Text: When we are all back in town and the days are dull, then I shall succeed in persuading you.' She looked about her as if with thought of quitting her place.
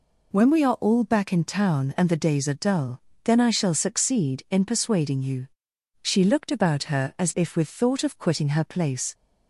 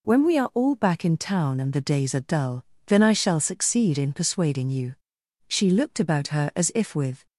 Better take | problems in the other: first | stops before "thought of quitting her place"; at 7.2 s

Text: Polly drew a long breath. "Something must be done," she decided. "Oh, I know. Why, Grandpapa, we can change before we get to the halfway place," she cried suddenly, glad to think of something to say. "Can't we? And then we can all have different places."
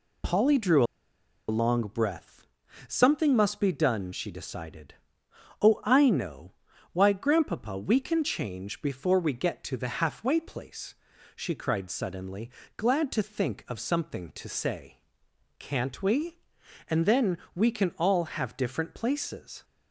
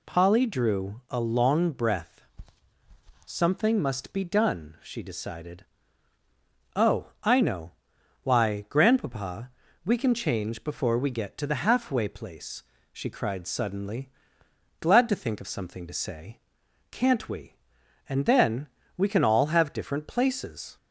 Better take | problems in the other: second | pauses between "drew" and "a"; noticeable; at 0.8 s; 0.65 s long // pauses between "then" and "we"; slight; at 17.3 s; 0.18 s long; slight in the second

